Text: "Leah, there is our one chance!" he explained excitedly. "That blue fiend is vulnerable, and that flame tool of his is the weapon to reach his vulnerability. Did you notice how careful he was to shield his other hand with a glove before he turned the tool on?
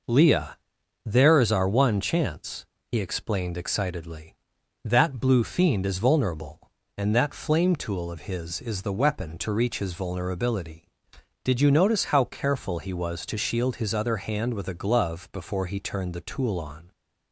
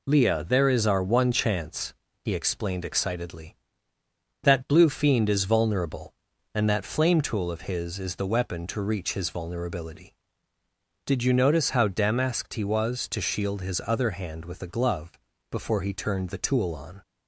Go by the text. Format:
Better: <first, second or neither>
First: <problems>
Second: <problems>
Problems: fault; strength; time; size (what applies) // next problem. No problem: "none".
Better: first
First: none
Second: says "damasked" for "careful"; at 11.8 s // pauses between "glove" and "before"; at 15.1 s; 0.38 s long